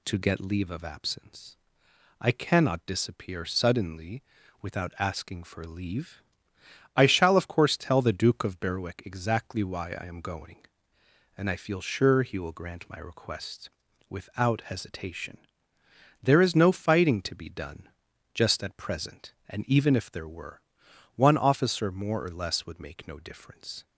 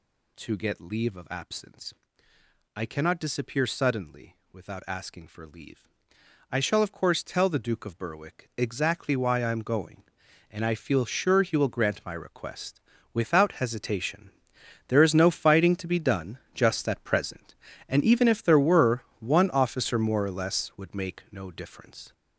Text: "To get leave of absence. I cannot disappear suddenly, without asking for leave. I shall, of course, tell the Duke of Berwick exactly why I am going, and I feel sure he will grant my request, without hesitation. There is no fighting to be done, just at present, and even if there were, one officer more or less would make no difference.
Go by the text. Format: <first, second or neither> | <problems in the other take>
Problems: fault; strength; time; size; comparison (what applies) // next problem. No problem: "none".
first | gets louder; strong; throughout; 7 dB